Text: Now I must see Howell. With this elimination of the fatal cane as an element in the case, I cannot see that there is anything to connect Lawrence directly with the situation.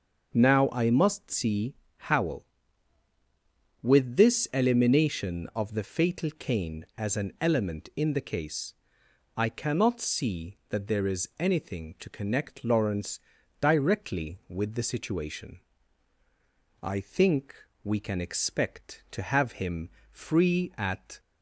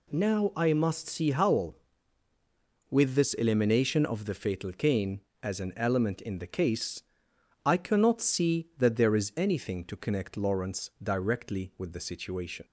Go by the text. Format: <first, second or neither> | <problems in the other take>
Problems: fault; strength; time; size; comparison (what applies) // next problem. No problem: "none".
second | starts louder than the rest; until 1.3 s; 6.5 dB // pauses between "see" and "Howell"; slight; at 1.7 s; 0.24 s long // pauses between "Lawrence" and "directly"; at 13.1 s; 0.40 s long // goes on to say "I think we can expect to have him free at"; strong; from 16.8 s on; 4.3 s long